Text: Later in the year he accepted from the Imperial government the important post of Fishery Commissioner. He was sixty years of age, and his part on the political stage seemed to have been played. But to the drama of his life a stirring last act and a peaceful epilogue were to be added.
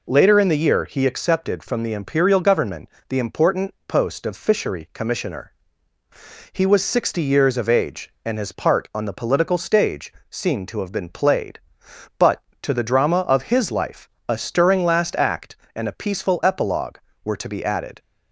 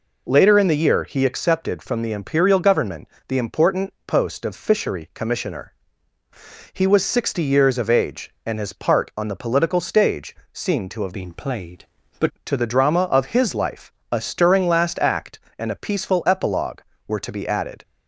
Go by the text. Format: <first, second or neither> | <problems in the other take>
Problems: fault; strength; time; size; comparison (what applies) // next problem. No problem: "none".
first | pauses between "government" and "the"; slight; at 3.0 s; 0.18 s long; slight in the first // pauses between "stage" and "seemed"; slight; at 10.3 s; 0.16 s long; slight in the first // changes voice from "been" to "But"; from 11.1 to 12.2 s; 1.1 s long // pauses between "life" and "a"; slight; at 13.9 s; 0.18 s long; slight in the first